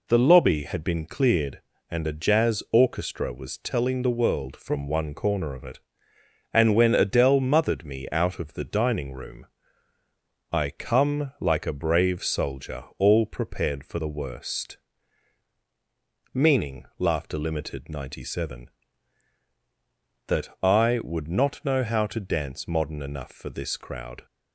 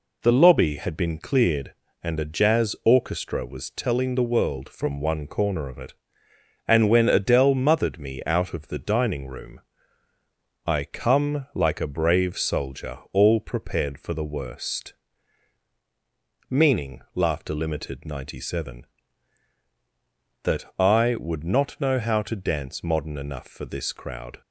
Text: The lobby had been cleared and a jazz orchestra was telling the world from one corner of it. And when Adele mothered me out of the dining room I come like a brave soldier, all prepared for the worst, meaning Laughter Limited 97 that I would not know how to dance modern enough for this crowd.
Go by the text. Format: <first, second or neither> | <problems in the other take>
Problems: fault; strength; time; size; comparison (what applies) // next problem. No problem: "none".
neither | pauses between "room" and "I"; the same in both // pauses between "meaning" and "Laughter"; slight; the same in both